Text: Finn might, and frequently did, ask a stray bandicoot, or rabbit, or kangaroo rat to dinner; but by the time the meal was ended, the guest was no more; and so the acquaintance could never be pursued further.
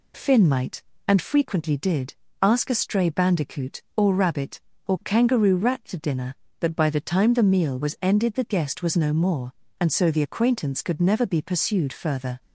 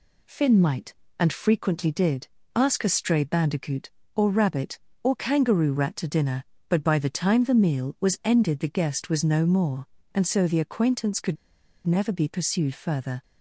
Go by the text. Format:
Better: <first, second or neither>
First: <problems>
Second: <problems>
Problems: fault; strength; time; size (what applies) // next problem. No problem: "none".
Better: first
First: none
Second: pauses between "could" and "never"; noticeable; at 11.3 s; 0.49 s long